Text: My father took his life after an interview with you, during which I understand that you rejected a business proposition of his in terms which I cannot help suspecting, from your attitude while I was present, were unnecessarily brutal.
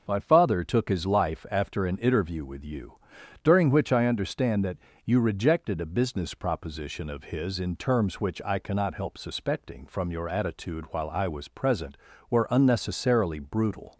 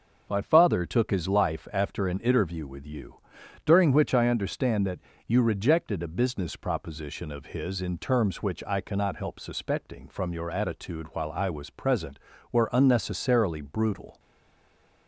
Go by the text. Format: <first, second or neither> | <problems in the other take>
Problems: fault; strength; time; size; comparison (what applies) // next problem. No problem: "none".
first | starts louder than the rest; until 1.2 s; 6.5 dB; also in the first // pauses between "that" and "you"; slight; at 4.9 s; 0.26 s long; slight in the first // stays silent after the last word; slight; from 14.1 s on; 0.9 s long